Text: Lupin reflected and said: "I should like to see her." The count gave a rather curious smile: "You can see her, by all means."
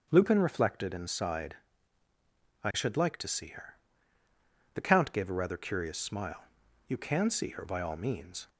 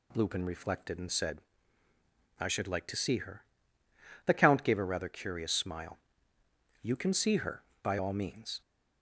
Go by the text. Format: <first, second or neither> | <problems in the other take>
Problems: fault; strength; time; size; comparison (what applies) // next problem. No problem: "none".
second | starts louder than the rest; until 1.1 s; 7 dB // says "sighed" for "said"; at 1.0 s